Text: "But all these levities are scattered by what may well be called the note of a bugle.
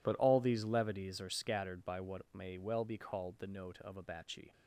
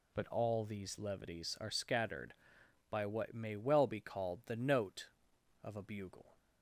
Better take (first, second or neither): second